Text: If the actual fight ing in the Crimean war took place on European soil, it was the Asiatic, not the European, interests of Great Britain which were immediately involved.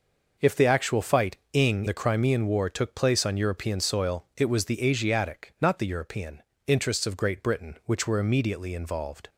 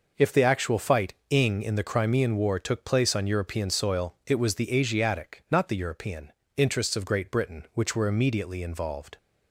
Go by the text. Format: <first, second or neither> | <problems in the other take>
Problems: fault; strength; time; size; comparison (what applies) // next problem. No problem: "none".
second | skips "in"; at 1.8 s